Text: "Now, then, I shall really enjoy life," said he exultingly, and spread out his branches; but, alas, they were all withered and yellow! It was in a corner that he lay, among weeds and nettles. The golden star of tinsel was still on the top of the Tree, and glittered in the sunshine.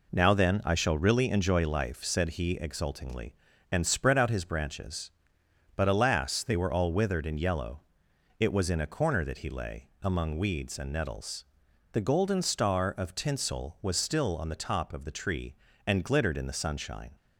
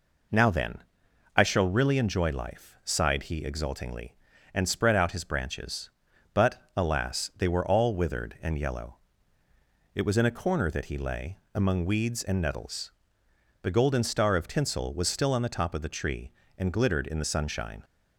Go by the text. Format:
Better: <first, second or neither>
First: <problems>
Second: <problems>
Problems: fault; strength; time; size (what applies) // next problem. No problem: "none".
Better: first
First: none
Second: says "sighed" for "said"; at 2.8 s